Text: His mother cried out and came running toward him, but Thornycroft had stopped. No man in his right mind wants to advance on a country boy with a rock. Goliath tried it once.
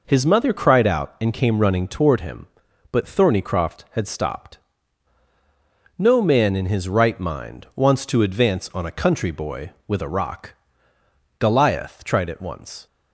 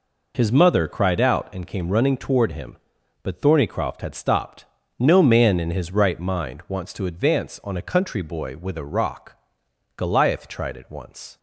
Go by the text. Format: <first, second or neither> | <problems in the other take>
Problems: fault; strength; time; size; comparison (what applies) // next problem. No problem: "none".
neither | none